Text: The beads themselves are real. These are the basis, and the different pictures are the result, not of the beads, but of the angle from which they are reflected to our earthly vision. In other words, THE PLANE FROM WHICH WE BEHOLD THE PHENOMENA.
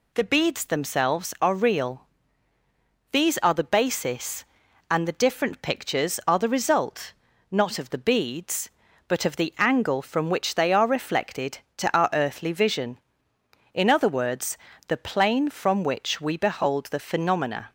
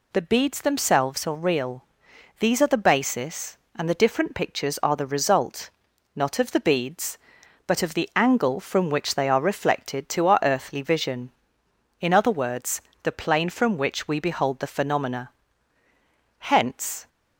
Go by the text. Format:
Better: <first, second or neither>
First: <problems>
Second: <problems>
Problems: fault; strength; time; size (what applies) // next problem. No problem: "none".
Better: first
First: none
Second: goes on to say "Hence"; noticeable; from 16.3 s on; 0.70 s long